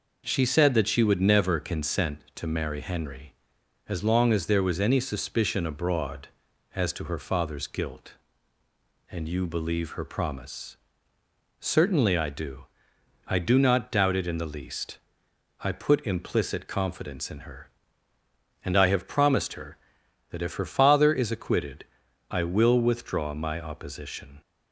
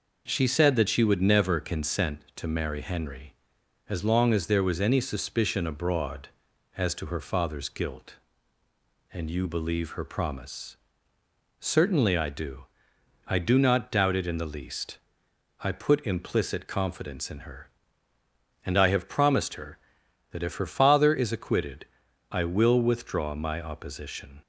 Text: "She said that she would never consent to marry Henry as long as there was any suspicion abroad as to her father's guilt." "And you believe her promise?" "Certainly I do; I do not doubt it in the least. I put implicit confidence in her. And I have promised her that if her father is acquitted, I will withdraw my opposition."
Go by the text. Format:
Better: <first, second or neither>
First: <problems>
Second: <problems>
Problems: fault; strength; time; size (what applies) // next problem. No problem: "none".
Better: neither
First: none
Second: none